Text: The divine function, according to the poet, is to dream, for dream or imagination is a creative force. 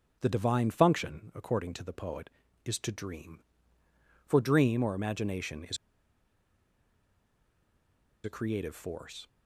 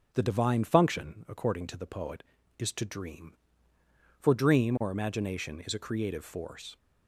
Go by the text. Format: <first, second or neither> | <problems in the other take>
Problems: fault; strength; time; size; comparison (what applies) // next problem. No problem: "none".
second | pauses between "is" and "a"; strong; at 5.7 s; 2.4 s long